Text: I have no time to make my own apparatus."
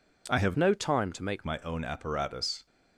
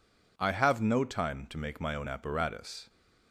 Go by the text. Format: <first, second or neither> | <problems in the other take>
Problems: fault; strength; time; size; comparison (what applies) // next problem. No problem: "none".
second | changes voice from "no" to "make"; from 0.5 to 1.4 s; 0.9 s long